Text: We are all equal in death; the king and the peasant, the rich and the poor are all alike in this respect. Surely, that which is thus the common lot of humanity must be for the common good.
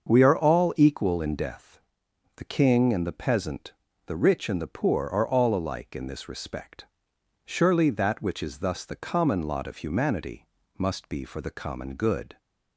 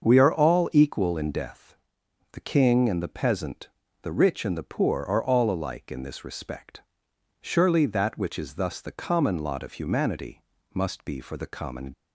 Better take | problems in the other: first | starts louder than the rest; until 1.1 s; 6.5 dB; also in the first // pauses between "humanity" and "must"; slight; at 10.4 s; 0.32 s long; slight in the first // stops before "good"; at 11.9 s

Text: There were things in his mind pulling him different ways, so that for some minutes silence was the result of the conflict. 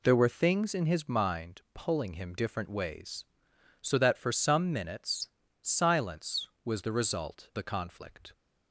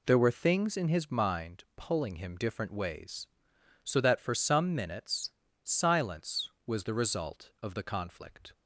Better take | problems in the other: second | pauses between "minutes" and "silence"; slight; at 5.2 s; 0.34 s long; slight in the second // skips "of"; at 7.5 s

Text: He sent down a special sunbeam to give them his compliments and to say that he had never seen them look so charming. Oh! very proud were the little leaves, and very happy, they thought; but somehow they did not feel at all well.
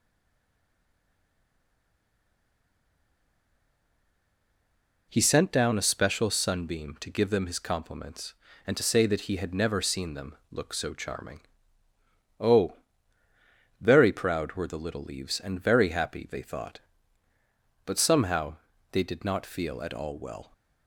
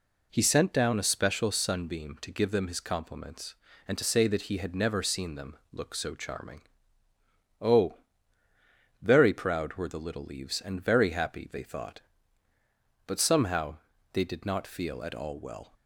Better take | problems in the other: second | stays silent before the first word; strong; until 5.1 s; 5.1 s long // pauses between "them" and "look"; slight; at 10.3 s; 0.16 s long; slight in the second // pauses between "somehow" and "they"; slight; at 18.5 s; 0.34 s long; slight in the second

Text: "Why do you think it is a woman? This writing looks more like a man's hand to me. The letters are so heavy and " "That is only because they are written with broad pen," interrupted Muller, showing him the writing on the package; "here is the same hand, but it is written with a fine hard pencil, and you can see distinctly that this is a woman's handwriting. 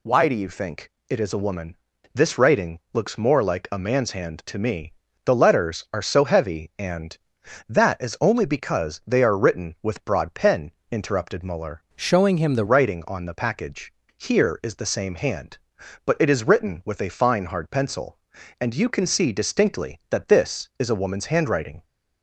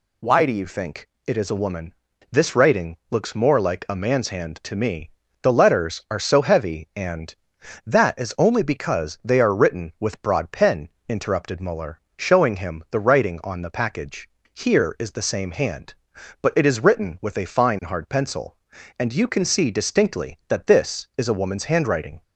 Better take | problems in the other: second | pauses between "think" and "it"; slight; at 0.9 s; 0.16 s long; slight in the second // changes voice from "showing" to "the"; from 11.9 to 12.6 s; 0.7 s long

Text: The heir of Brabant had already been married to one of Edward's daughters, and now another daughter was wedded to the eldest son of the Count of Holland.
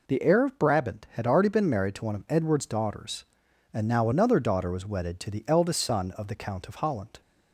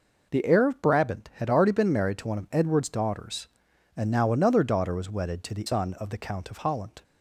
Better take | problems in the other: first | skips "eldest"; at 5.6 s

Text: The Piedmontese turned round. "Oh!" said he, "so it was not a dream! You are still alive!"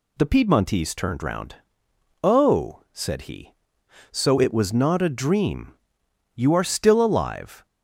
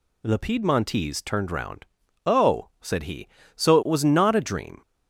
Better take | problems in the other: first | stops before "You are still alive"; at 4.8 s

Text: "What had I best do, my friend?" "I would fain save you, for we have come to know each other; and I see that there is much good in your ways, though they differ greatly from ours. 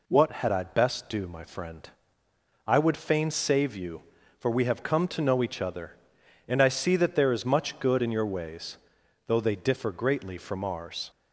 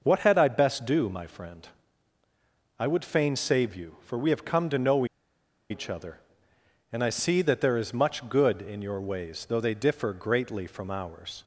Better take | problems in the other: first | pauses between "know" and "each"; noticeable; at 5.0 s; 0.65 s long

